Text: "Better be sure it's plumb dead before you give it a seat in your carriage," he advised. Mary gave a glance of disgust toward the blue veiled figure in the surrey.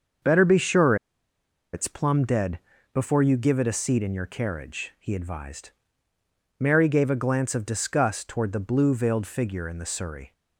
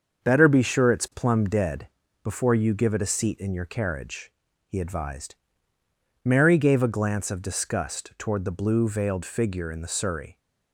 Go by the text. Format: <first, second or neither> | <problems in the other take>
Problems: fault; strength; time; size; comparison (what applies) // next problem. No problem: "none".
second | starts louder than the rest; until 2.0 s; 6.5 dB; also in the second // pauses between "sure" and "it's"; noticeable; at 0.9 s; 0.78 s long // pauses between "dead" and "before"; slight; at 2.5 s; 0.34 s long; slight in the second